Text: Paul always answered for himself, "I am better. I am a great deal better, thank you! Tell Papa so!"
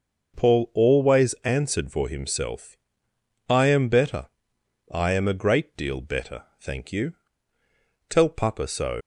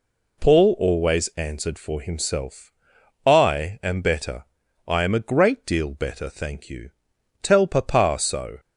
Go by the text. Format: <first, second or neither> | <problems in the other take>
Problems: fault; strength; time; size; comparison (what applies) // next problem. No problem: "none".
second | leaves "so" unfinished; at 9.0 s; 70 ms